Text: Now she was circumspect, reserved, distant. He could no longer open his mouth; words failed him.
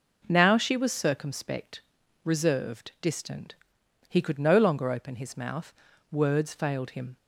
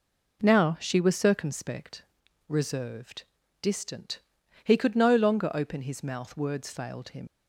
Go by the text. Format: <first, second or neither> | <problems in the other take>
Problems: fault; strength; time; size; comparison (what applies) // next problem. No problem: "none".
first | leaves "him" unfinished; at 7.2 s; 90 ms